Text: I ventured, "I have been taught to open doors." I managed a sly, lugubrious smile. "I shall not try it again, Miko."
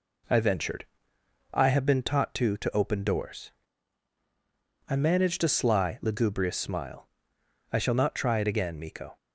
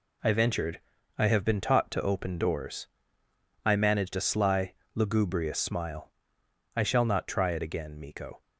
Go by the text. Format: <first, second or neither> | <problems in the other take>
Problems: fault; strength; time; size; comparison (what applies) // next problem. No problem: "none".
second | says "to" twice; at 2.5 s